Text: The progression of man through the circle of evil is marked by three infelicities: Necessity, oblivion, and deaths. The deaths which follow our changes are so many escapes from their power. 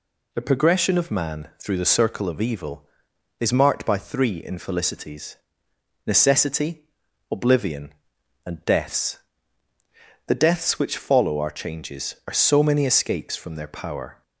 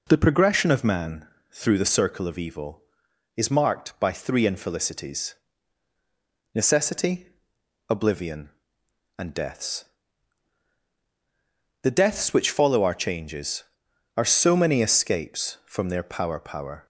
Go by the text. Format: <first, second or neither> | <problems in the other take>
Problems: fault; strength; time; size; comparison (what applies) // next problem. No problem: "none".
first | pauses between "man" and "through"; slight; at 1.2 s; 0.24 s long // says "power" twice; at 16.3 s